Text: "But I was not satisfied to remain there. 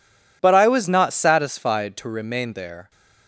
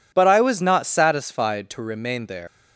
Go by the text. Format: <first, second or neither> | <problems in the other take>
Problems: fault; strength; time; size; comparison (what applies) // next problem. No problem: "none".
first | leaves "there" unfinished; at 2.4 s; 160 ms